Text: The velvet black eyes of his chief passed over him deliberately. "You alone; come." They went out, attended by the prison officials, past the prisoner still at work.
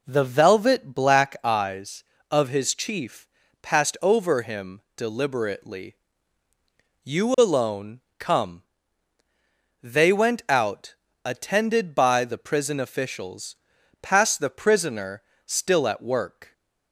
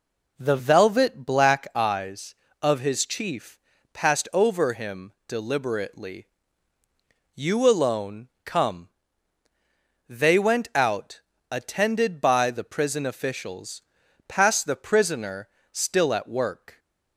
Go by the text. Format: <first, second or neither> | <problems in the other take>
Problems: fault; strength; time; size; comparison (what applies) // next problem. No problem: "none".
neither | pauses between "chief" and "passed"; slight; the same in both // pauses between "him" and "deliberately"; slight; the same in both // pauses between "prisoner" and "still"; slight; the same in both